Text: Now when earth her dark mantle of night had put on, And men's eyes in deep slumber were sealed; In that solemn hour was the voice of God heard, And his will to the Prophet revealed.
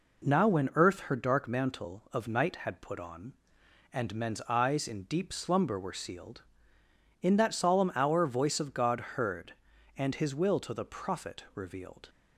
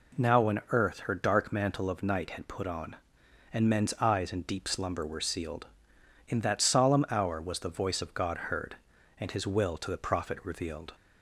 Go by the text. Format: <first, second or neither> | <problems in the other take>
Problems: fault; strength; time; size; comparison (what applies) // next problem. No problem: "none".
second | skips "was the"; at 8.2 s